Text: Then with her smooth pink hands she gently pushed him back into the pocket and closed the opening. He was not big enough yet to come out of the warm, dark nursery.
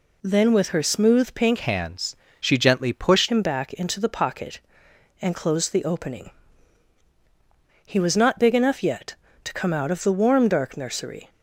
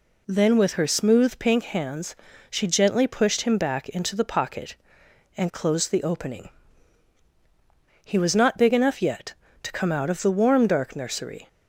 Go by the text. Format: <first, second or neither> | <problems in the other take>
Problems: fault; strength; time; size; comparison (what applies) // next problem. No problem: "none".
second | changes voice from "hands" to "pushed"; from 1.5 to 3.2 s; 1.7 s long // pauses between "hands" and "she"; slight; at 2.1 s; 0.24 s long; slight in the second